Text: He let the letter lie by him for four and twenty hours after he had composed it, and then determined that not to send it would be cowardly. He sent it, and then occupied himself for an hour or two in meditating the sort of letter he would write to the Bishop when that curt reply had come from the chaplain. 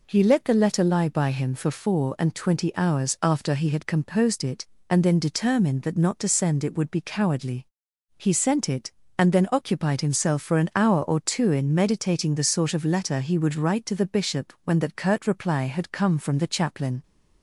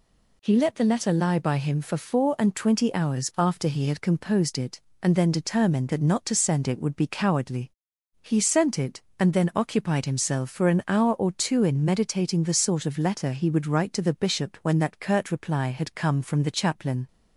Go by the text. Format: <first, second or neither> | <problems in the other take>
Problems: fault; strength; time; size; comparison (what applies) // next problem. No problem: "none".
neither | none